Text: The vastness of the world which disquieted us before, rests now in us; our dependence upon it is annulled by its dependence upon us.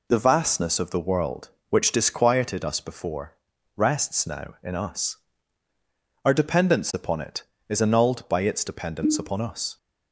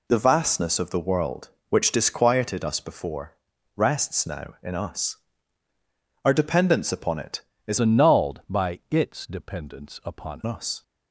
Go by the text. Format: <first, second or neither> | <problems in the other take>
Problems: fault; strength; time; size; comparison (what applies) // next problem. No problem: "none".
first | changes voice from "annulled" to "upon"; from 7.7 to 10.4 s; 2.7 s long